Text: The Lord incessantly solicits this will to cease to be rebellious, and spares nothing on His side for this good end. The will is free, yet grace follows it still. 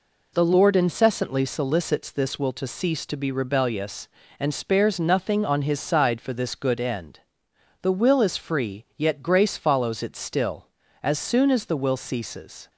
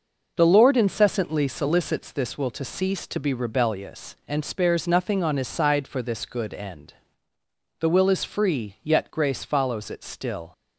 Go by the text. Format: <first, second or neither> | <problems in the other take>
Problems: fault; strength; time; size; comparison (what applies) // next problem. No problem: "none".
second | goes on to say "As soon as the will ceases"; strong; from 11.0 s on; 1.6 s long